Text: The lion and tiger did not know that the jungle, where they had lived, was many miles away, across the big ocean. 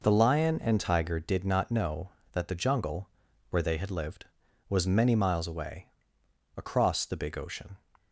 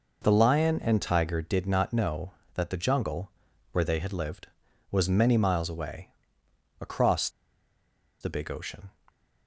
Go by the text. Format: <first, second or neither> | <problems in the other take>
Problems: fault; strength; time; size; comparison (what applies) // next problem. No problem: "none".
first | pauses between "across" and "the"; noticeable; at 7.2 s; 0.92 s long